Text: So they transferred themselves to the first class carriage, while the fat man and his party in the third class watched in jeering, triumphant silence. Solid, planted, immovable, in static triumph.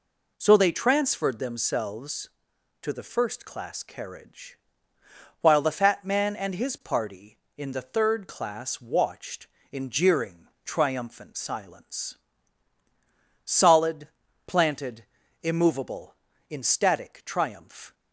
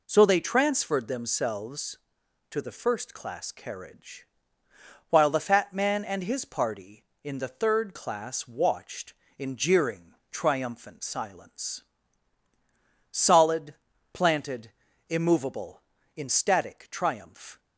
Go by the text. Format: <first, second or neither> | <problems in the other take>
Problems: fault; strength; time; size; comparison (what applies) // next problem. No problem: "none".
neither | none